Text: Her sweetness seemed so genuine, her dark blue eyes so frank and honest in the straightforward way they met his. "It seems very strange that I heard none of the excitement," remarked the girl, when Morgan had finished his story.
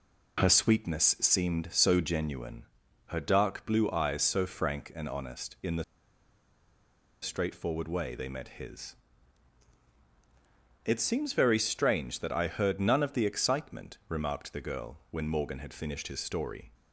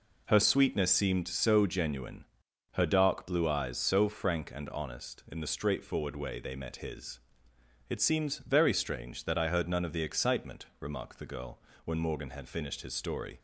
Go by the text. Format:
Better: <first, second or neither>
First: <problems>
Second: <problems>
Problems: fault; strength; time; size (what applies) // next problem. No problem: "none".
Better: second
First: pauses between "the" and "straightforward"; strong; at 5.8 s; 1.3 s long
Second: none